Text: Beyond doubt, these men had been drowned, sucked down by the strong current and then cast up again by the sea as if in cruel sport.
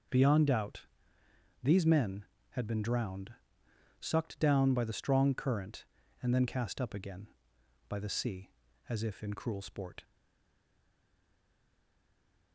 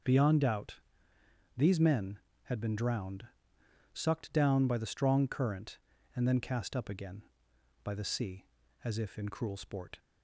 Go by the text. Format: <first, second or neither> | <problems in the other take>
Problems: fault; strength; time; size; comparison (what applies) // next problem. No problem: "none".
second | stays silent after the last word; from 10.0 s on; 2.5 s long